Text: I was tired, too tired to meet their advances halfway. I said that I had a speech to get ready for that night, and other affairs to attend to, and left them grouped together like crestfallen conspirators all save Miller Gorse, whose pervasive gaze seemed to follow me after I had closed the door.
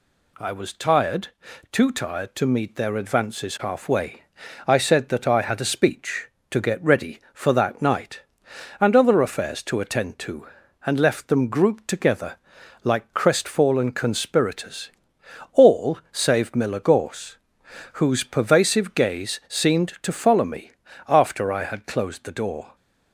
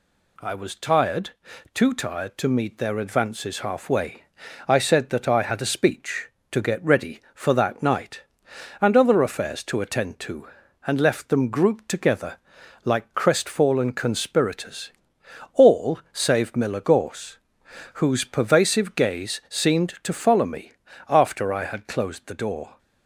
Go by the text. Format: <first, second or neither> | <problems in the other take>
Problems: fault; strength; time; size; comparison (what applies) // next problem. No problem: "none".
neither | pauses between "together" and "like"; noticeable; the same in both // pauses between "conspirators" and "all"; noticeable; the same in both // pauses between "me" and "after"; the same in both